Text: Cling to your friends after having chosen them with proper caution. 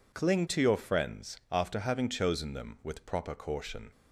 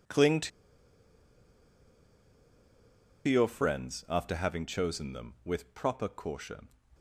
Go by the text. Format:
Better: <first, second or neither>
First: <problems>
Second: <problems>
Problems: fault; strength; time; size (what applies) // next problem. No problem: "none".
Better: first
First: none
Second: pauses between "to" and "your"; strong; at 0.5 s; 2.7 s long